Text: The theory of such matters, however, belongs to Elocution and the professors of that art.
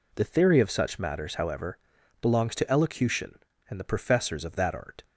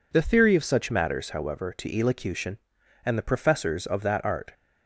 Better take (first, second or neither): first